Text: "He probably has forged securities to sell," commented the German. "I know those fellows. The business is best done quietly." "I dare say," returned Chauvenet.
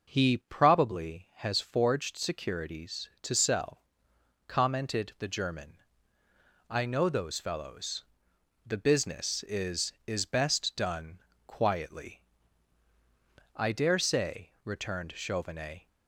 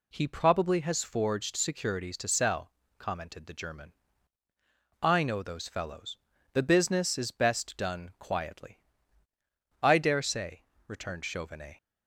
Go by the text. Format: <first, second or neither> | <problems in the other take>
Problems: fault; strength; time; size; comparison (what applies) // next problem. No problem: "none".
second | says "is" twice; at 10.0 s // pauses between "done" and "quietly"; slight; at 11.1 s; 0.26 s long